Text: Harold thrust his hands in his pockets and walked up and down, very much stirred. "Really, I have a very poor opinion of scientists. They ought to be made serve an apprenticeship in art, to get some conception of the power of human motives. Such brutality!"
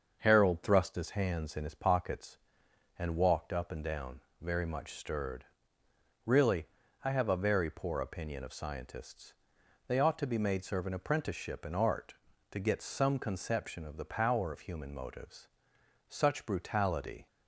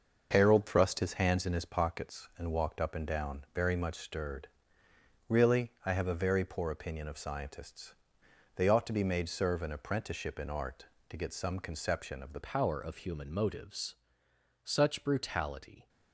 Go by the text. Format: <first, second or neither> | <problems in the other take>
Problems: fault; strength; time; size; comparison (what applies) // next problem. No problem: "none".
first | starts louder than the rest; until 1.3 s; 6 dB; also in the first // changes voice at "power"; from 12.4 s on; 3.4 s long